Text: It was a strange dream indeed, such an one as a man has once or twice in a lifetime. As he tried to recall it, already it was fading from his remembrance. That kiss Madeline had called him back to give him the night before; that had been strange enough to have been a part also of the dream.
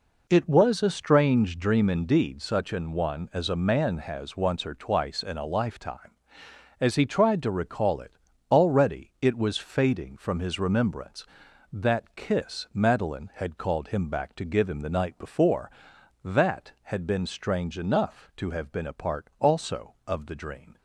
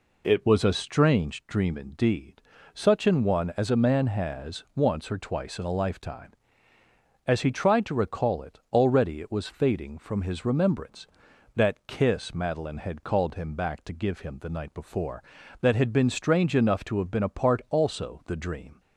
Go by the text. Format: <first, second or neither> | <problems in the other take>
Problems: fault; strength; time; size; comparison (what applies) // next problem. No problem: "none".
first | skips "of"; at 18.2 s